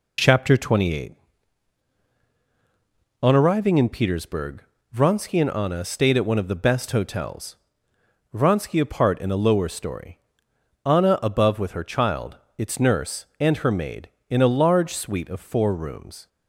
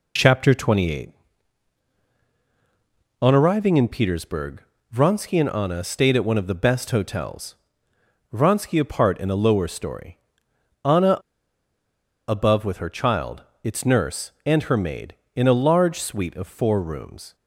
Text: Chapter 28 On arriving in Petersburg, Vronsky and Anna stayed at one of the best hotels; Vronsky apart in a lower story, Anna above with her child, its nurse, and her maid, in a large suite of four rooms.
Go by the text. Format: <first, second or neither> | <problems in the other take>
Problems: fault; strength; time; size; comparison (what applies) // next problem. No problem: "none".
first | pauses between "Anna" and "above"; at 11.1 s; 1.0 s long